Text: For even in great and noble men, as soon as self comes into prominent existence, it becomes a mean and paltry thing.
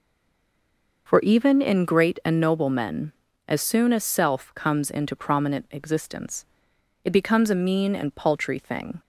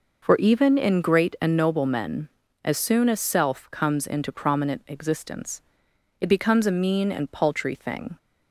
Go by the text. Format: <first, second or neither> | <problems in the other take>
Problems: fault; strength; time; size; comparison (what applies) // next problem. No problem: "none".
second | stays silent before the first word; until 1.0 s; 1.0 s long